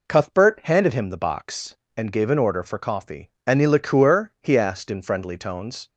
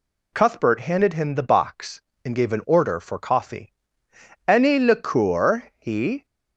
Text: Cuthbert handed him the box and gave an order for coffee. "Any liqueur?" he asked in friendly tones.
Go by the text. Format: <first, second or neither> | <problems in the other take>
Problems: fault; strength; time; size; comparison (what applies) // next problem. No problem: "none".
first | stops before "asked in friendly tones"; at 6.2 s